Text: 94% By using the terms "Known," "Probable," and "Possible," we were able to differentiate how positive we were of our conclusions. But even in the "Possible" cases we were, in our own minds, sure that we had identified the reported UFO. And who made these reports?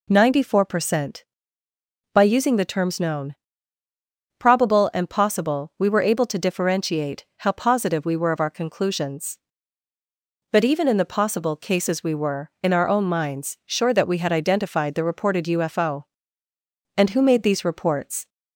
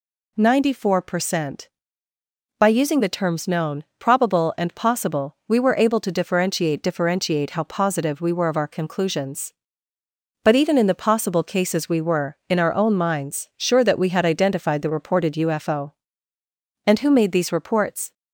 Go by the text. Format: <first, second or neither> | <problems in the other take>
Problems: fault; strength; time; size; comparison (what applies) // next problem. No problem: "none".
first | says "differentiate" twice; at 6.8 s